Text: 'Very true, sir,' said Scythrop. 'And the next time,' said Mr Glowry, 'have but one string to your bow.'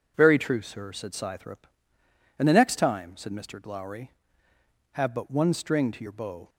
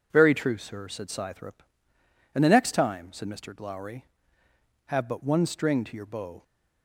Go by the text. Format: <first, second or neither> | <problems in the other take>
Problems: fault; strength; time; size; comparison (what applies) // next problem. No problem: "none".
neither | none